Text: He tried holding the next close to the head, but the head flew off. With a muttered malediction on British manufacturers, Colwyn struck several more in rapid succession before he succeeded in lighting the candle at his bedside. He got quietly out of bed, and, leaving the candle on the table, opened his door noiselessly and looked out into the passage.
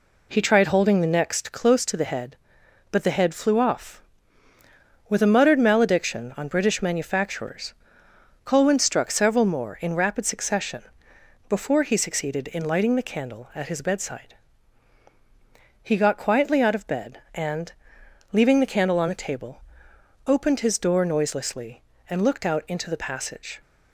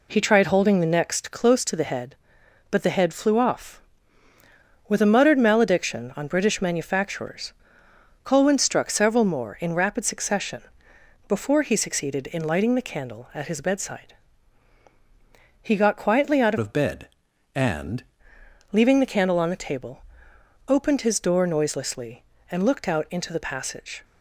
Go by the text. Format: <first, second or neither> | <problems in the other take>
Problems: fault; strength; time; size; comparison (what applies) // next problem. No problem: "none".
first | pauses between "succession" and "before"; noticeable; at 10.6 s; 0.64 s long; noticeable in the first // changes voice from "of" to "and"; from 16.5 to 18.0 s; 1.5 s long